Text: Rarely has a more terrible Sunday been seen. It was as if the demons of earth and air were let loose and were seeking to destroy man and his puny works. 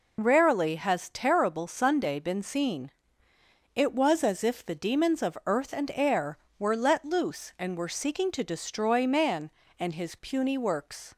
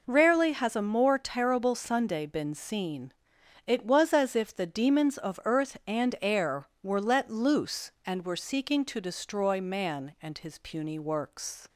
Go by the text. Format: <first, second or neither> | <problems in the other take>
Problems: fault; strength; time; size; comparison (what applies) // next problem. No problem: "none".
second | skips "a more"; at 1.0 s